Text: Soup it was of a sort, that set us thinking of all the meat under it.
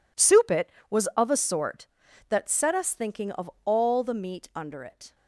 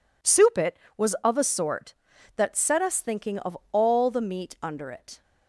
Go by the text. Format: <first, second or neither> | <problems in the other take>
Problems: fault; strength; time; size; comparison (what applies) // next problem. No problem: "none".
second | gets quieter; strong; throughout; 14 dB